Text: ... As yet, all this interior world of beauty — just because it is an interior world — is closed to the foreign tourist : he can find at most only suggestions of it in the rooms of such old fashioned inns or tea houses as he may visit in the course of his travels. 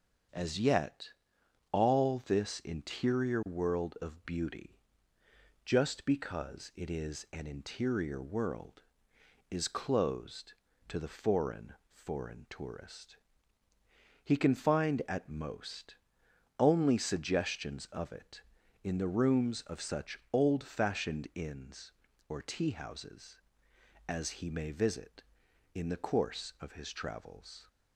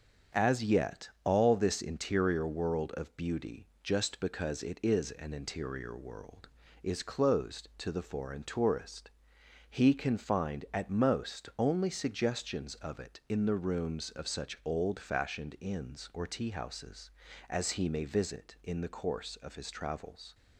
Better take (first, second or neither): second